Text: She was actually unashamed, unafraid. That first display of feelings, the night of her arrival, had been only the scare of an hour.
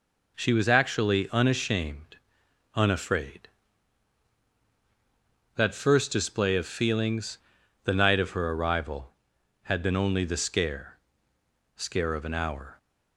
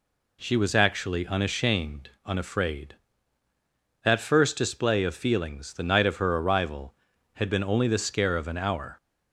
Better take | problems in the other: second | says "scare" twice; at 11.7 s

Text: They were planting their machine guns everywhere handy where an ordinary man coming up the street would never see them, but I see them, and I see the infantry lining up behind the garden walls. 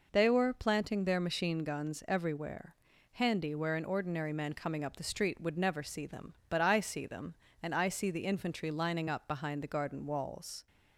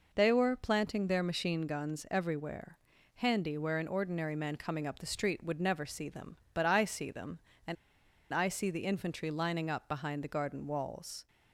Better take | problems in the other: first | pauses between "everywhere" and "handy"; at 2.7 s; 0.38 s long; also in the first // pauses between "and" and "I"; noticeable; at 7.7 s; 0.57 s long

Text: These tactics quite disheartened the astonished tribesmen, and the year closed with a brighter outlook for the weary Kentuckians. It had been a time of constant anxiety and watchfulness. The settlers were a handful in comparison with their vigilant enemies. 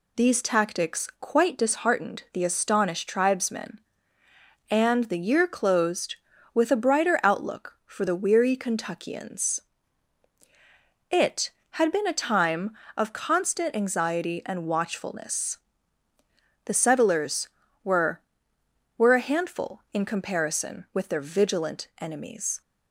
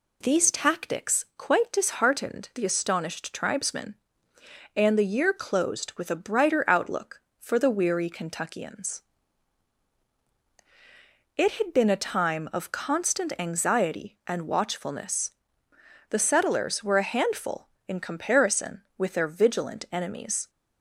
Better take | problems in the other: second | says "were" twice; at 18.9 s

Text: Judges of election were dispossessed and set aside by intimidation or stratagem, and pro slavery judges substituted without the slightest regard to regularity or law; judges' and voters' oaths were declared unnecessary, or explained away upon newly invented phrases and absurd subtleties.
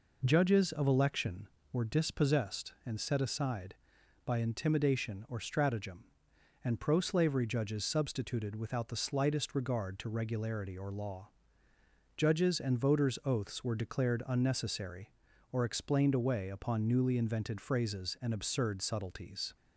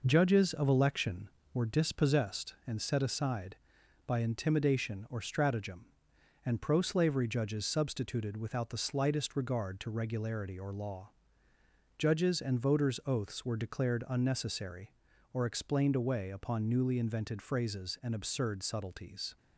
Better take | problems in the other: first | gets quieter; noticeable; throughout; 4 dB

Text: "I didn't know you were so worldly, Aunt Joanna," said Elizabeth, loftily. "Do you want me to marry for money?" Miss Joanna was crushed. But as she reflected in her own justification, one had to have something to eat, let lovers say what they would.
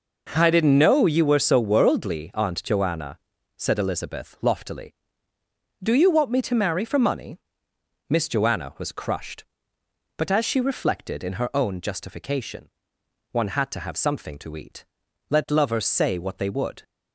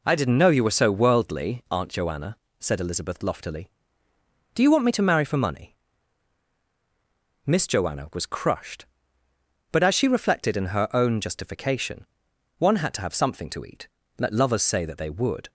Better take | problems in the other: first | says "that" for "what"; at 14.8 s

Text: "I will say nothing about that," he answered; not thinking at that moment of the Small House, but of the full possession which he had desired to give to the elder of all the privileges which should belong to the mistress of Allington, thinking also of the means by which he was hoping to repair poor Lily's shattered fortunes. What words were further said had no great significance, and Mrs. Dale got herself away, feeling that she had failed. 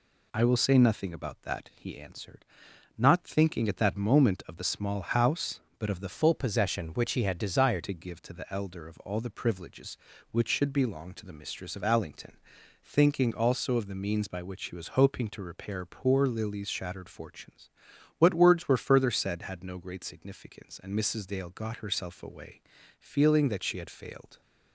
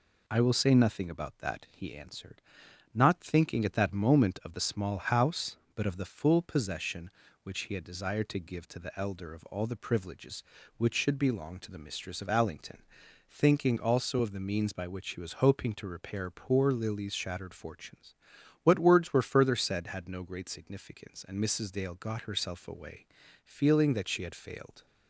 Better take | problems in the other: second | changes voice from "full" to "desired"; from 6.1 to 7.8 s; 1.7 s long

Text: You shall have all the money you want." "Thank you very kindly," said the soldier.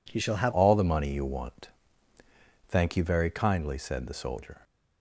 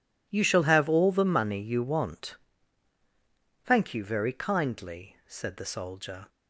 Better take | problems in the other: second | changes voice at "all"; from 0.5 s on; 4.1 s long

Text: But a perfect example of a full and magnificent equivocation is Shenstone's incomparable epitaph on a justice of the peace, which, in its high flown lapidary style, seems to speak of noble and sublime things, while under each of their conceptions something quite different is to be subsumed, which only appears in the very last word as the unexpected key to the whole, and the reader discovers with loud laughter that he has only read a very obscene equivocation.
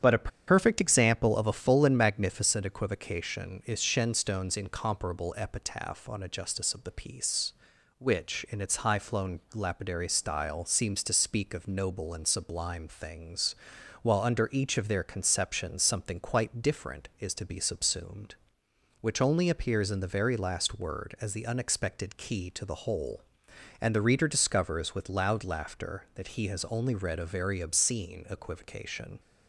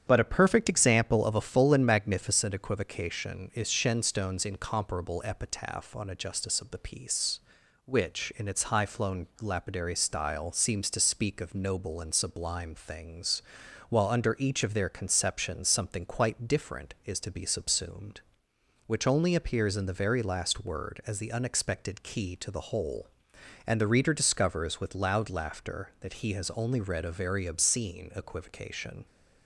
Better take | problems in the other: second | starts louder than the rest; strong; until 1.1 s; 9 dB; strong in the second // pauses between "a" and "perfect"; slight; at 0.3 s; 0.17 s long

